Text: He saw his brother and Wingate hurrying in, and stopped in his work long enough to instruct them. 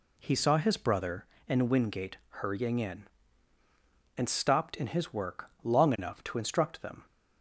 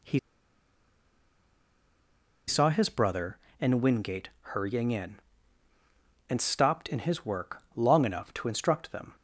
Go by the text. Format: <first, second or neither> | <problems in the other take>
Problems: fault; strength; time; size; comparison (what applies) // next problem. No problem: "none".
first | pauses between "He" and "saw"; strong; at 0.1 s; 2.3 s long